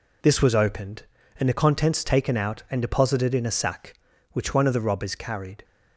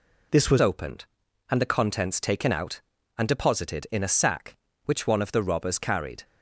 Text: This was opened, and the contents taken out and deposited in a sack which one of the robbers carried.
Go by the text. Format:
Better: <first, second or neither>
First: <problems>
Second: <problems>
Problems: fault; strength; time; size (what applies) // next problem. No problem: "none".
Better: first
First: none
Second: changes voice at "opened"; from 0.6 s on; 5.6 s long